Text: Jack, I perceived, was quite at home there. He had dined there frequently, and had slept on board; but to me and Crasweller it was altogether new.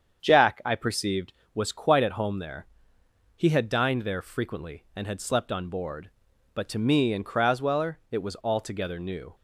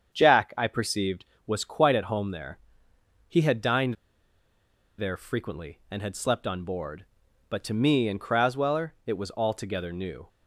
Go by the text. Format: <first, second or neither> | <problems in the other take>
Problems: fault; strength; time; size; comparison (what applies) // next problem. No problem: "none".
first | starts louder than the rest; strong; until 1.1 s; 7.5 dB; strong in the first // pauses between "dined" and "there"; at 3.9 s; 1.0 s long